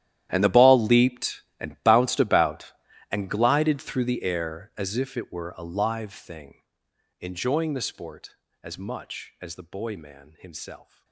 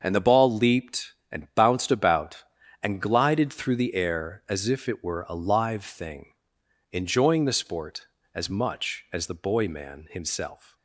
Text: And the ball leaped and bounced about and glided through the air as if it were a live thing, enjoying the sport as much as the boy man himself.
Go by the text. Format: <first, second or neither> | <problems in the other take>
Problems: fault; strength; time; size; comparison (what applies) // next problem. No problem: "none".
second | gets quieter; strong; throughout; 19 dB // starts louder than the rest; strong; until 1.3 s; 12 dB; also in the second